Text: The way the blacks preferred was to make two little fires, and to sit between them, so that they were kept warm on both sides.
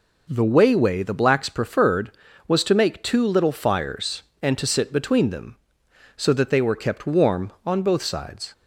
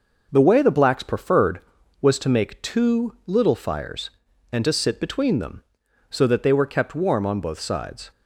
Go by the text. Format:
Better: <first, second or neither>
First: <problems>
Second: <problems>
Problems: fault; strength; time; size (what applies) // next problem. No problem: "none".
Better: second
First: says "way" twice; at 0.7 s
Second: none